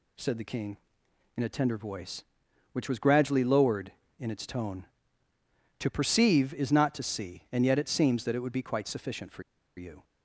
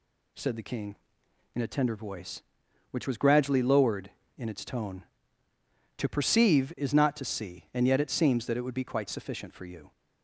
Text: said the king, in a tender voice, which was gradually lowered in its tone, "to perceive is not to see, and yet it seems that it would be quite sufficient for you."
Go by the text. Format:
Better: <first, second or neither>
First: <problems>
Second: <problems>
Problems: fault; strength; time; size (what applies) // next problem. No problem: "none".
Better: second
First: pauses between "for" and "you"; slight; at 9.4 s; 0.34 s long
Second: none